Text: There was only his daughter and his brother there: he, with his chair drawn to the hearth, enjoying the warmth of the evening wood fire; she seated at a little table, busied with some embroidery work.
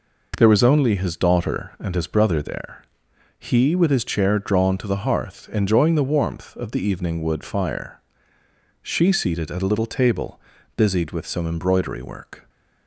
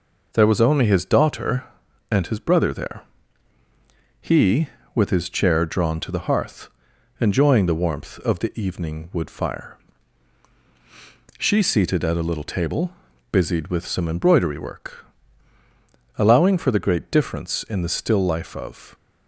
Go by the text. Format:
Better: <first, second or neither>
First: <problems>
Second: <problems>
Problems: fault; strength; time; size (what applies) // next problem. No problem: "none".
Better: first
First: none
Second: goes on to say "Allowing for the great difference in the still life of"; strong; from 16.1 s on; 2.7 s long